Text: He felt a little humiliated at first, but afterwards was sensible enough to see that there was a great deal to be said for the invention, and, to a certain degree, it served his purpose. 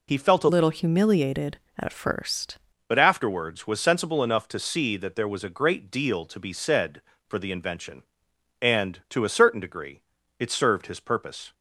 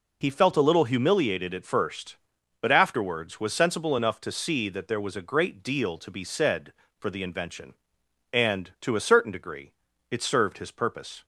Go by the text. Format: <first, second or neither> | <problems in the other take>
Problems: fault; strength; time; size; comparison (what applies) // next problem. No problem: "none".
second | changes voice from "little" to "first"; from 0.4 to 2.5 s; 2.1 s long